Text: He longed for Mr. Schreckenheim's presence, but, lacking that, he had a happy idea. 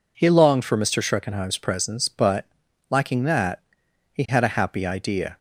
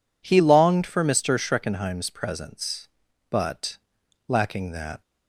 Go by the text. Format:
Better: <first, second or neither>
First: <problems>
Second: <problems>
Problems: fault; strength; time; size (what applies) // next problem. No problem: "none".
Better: first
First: none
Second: stops before "he had a happy idea"; at 5.0 s